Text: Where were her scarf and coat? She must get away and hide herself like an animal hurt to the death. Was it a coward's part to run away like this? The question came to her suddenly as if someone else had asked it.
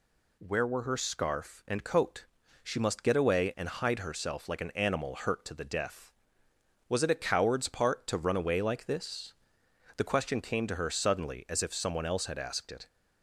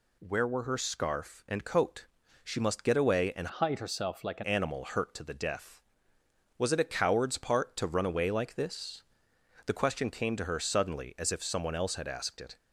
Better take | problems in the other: first | changes voice from "hide" to "an"; from 3.5 to 4.4 s; 0.9 s long

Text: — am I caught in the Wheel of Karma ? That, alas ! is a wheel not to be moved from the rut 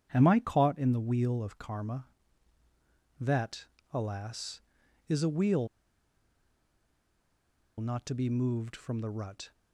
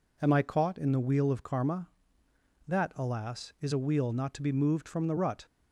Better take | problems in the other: second | starts louder than the rest; strong; until 1.1 s; 9 dB // pauses between "wheel" and "not"; strong; at 5.6 s; 2.1 s long

